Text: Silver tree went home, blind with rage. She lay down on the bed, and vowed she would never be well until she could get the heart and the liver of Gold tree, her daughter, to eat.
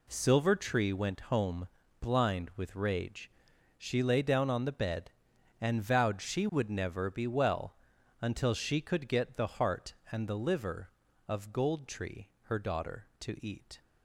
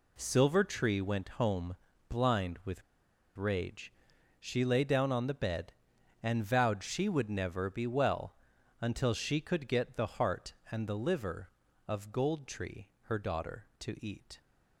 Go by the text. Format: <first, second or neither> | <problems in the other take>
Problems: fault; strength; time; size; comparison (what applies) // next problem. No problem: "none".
first | pauses between "with" and "rage"; noticeable; at 2.8 s; 0.54 s long // pauses between "well" and "until"; at 8.3 s; 0.44 s long; also in the first